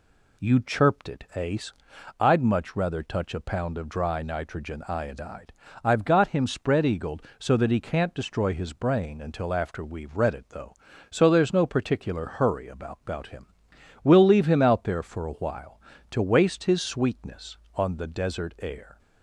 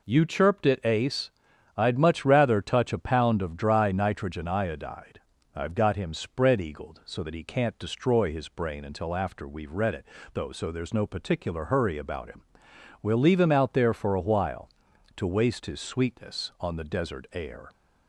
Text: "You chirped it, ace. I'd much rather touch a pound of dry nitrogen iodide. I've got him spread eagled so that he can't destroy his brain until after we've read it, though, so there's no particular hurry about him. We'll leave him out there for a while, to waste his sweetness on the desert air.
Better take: second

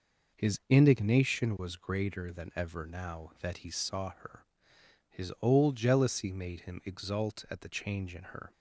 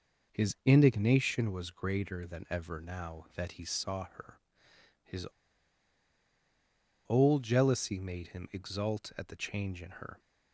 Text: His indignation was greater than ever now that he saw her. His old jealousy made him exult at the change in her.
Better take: first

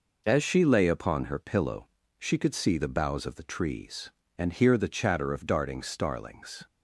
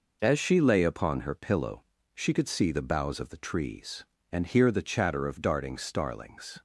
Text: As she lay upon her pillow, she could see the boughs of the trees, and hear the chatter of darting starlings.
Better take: neither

